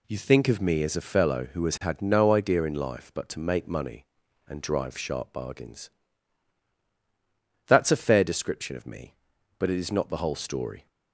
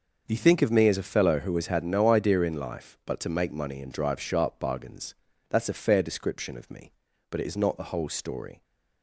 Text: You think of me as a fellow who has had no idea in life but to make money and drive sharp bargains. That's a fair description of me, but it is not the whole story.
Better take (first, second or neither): neither